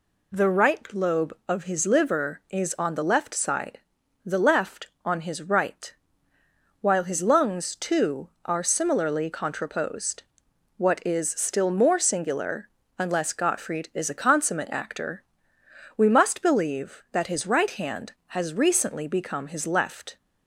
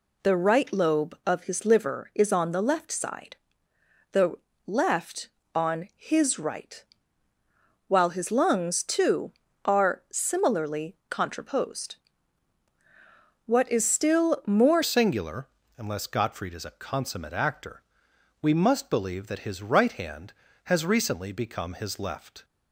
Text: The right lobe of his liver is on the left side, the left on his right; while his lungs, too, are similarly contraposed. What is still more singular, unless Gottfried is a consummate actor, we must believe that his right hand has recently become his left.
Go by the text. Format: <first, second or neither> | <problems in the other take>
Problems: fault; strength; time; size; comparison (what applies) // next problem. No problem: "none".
first | pauses between "the" and "left"; slight; at 4.3 s; 0.32 s long // changes voice at "singular"; from 14.8 s on; 7.6 s long